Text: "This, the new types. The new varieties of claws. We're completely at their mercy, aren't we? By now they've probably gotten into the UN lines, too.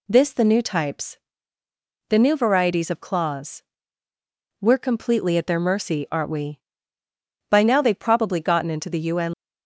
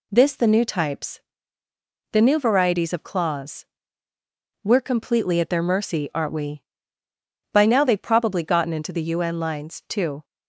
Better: second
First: stops before "lines too"; at 9.3 s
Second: none

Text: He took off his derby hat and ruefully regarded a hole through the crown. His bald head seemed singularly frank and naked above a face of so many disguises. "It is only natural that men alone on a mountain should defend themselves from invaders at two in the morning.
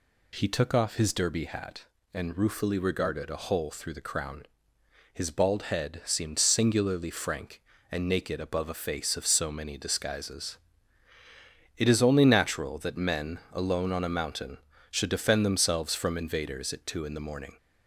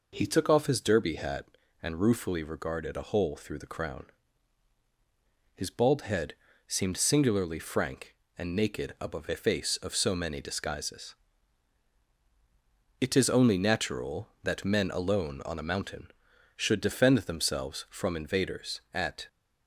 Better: first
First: none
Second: pauses between "head" and "seemed"; slight; at 6.3 s; 0.32 s long // stops before "two in the morning"; at 19.2 s

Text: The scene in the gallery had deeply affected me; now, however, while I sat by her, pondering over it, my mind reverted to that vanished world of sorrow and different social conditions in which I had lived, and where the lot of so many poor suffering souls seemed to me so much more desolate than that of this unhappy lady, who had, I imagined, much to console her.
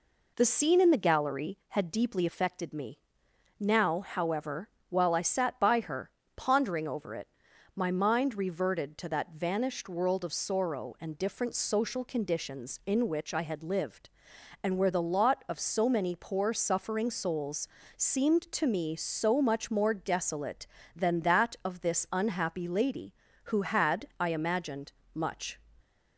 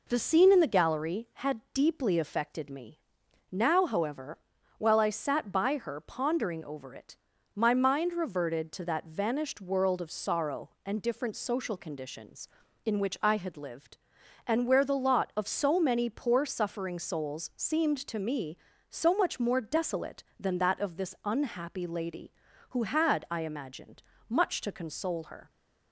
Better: second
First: pauses between "souls" and "seemed"; slight; at 17.6 s; 0.30 s long // stops before "to console her"; at 25.8 s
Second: none

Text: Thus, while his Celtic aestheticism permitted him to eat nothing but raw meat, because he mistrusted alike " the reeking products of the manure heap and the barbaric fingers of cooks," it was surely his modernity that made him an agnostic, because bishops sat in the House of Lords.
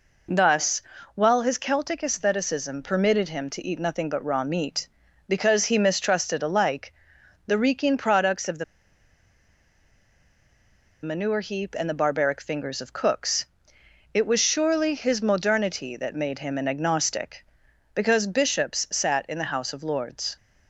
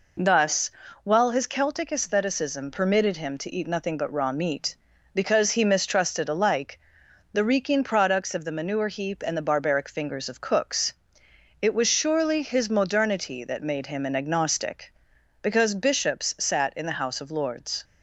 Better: second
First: pauses between "the" and "manure"; strong; at 8.6 s; 2.3 s long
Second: none

